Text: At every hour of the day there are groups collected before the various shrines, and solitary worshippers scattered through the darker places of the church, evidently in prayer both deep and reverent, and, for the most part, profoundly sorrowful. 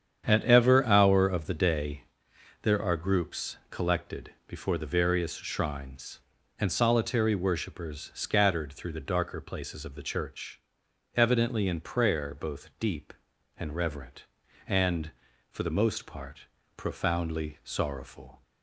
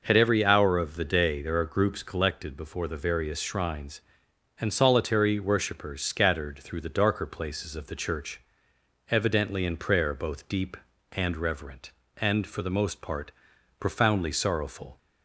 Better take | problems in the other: second | starts louder than the rest; strong; until 1.3 s; 8.5 dB // says "ever" for "every"; at 0.4 s // pauses between "day" and "there"; noticeable; at 2.0 s; 0.56 s long // pauses between "collected" and "before"; slight; at 4.3 s; 0.16 s long

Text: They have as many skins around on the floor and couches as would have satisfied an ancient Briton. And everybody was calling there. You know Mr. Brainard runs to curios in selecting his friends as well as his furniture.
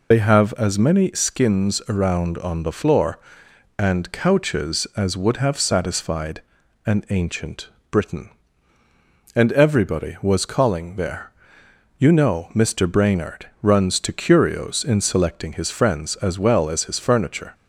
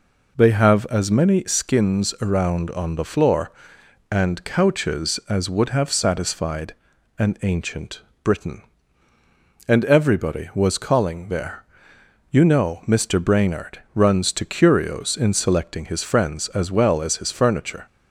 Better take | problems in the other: second | loses the start of "They"; at 0.1 s; 70 ms // pauses between "satisfied" and "an"; at 6.4 s; 0.44 s long; also in the second // pauses between "ancient" and "Briton"; slight; at 7.6 s; 0.22 s long; slight in the second

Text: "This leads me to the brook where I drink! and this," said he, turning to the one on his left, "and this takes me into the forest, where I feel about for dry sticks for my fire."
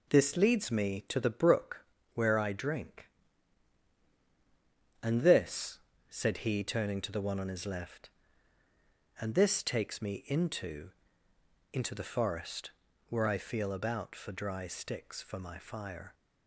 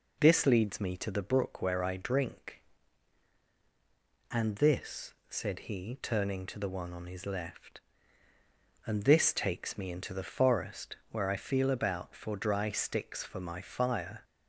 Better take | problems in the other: second | pauses between "brook" and "where"; slight; at 1.8 s; 0.30 s long // says "into" twice; at 11.7 s

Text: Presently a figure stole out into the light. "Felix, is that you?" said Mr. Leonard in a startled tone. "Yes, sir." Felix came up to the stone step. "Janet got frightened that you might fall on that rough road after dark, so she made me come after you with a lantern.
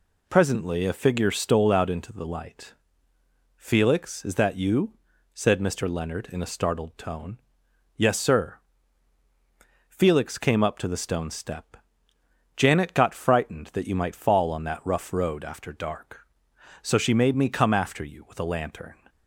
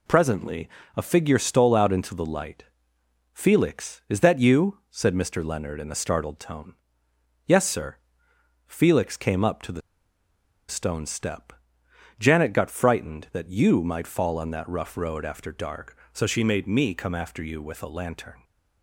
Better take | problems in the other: first | pauses between "Presently" and "a"; slight; at 0.6 s; 0.28 s long // pauses between "the" and "stone"; noticeable; at 9.8 s; 0.88 s long

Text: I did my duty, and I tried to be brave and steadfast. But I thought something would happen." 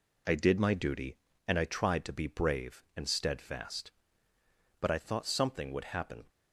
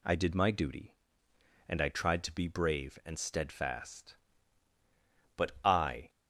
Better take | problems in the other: first | stops before "thought something would happen"; at 6.0 s

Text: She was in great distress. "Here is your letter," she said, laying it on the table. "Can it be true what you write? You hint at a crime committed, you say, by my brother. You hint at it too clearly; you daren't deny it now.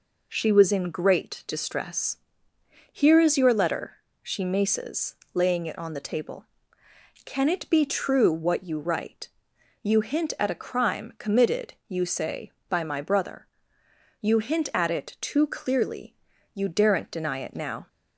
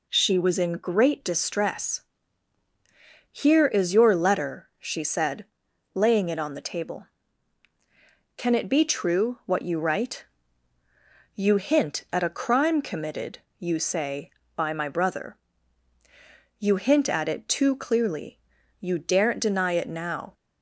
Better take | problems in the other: second | says "maces" for "said"; at 4.4 s

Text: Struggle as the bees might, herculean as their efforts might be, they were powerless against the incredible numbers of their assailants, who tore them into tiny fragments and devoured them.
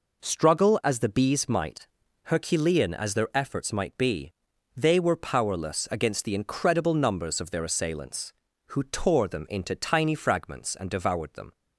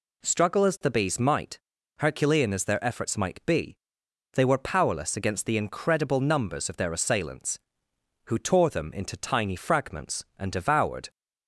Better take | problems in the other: first | stops before "them"; at 11.1 s

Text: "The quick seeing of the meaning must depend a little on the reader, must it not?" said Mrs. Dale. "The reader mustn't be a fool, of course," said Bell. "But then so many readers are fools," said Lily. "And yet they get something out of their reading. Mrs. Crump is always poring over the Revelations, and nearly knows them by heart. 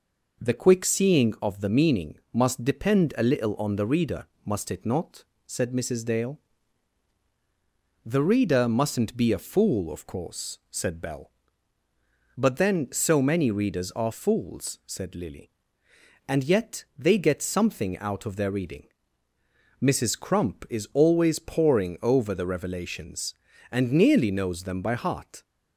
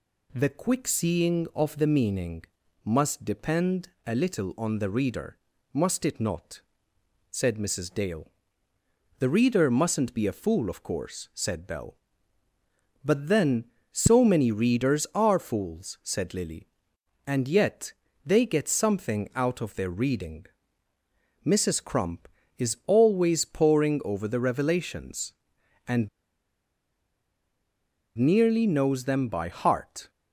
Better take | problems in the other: first | pauses between "meaning" and "must"; at 2.4 s; 0.40 s long // pauses between "depend" and "a"; slight; at 3.8 s; 0.18 s long // pauses between "yet" and "they"; slight; at 17.9 s; 0.34 s long // pauses between "and" and "nearly"; strong; at 26.0 s; 2.0 s long

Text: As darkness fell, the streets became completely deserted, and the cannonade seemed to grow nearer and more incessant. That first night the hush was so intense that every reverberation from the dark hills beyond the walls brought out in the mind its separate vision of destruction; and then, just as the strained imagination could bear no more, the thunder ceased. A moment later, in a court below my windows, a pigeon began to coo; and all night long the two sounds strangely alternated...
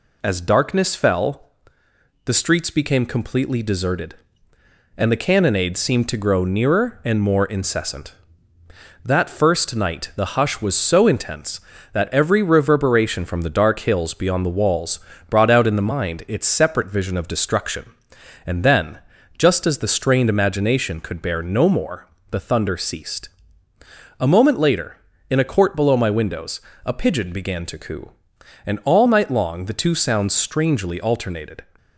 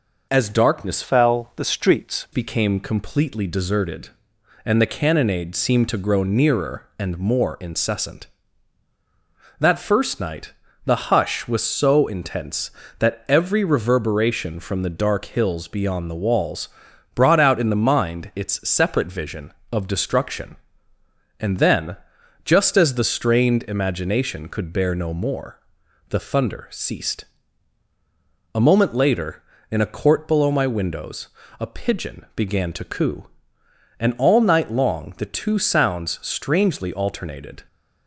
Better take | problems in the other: first | changes voice from "fell" to "streets"; from 1.0 to 2.2 s; 1.2 s long // pauses between "night" and "the"; slight; at 10.5 s; 0.34 s long // pauses between "walls" and "brought"; at 16.6 s; 0.44 s long; slight in the first

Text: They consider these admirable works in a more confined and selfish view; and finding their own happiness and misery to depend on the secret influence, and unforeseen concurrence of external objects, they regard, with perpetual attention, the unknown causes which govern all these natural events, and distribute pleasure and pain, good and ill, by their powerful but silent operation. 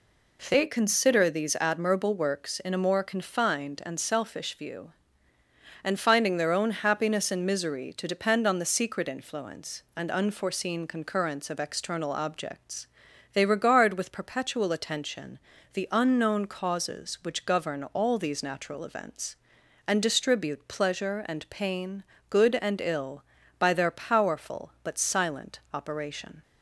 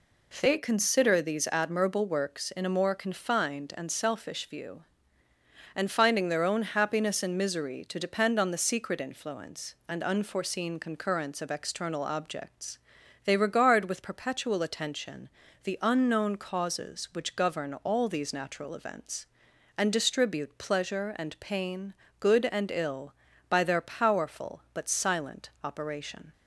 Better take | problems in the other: neither | none

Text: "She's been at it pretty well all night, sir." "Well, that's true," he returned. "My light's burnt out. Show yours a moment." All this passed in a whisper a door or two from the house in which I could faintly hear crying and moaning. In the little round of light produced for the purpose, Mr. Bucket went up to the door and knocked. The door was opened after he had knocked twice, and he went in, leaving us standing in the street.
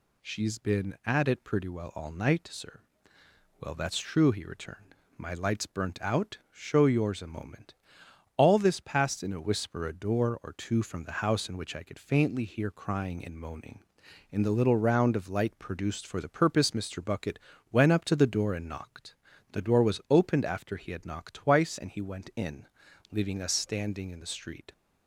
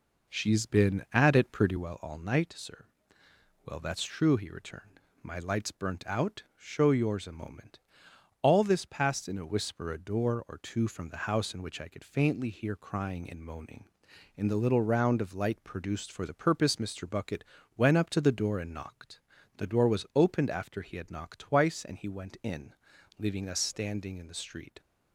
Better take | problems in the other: first | starts louder than the rest; noticeable; until 2.0 s; 4 dB // pauses between "Bucket" and "went"; slight; at 17.4 s; 0.32 s long; slight in the first

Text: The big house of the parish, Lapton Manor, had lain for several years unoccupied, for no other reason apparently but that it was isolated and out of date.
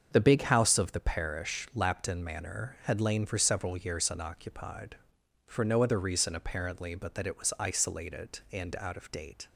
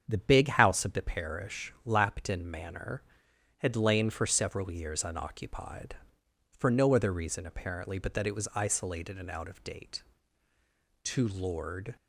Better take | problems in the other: first | starts louder than the rest; strong; until 1.0 s; 7.5 dB; also in the first // goes on to say "To Lord"; noticeable; from 11.0 s on; 0.92 s long

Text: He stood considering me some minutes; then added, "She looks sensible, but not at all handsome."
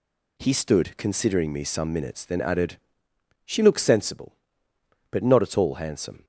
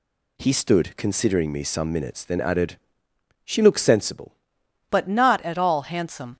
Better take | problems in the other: first | changes voice at "but"; from 4.8 s on; 1.5 s long

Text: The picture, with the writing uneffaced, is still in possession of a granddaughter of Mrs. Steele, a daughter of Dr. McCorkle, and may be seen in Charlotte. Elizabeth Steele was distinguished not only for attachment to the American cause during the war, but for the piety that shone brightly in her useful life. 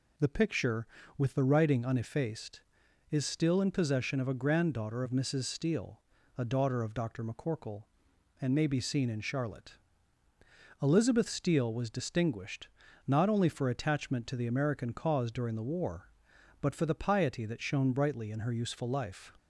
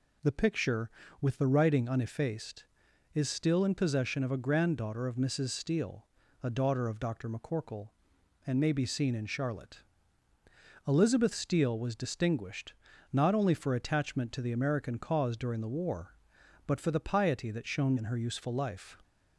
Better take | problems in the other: first | pauses between "distinguished" and "not"; at 12.7 s; 0.40 s long; also in the first // skips "brightly"; at 17.9 s

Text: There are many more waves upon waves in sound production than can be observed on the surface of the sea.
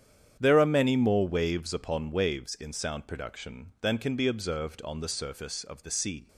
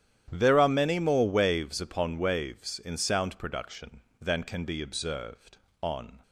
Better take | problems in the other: first | starts louder than the rest; strong; until 1.3 s; 10.5 dB; strong in the first // stops before "the surface of the sea"; at 6.2 s

